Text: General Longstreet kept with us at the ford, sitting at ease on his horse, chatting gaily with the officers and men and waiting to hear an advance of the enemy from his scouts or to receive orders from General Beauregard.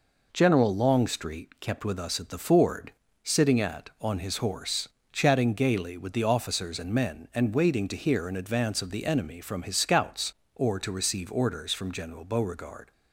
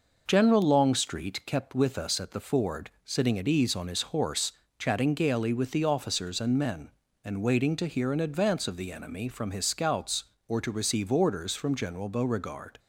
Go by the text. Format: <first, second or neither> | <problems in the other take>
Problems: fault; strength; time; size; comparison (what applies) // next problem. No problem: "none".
second | skips "ease"; at 3.9 s